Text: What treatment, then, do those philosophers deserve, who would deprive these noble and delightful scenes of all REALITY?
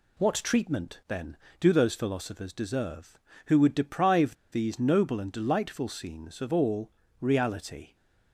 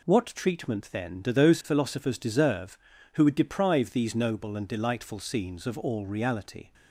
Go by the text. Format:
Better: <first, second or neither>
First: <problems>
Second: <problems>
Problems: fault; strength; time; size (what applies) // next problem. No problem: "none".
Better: second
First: pauses between "deprive" and "these"; slight; at 4.3 s; 0.19 s long // pauses between "all" and "REALITY"; slight; at 6.8 s; 0.32 s long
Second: none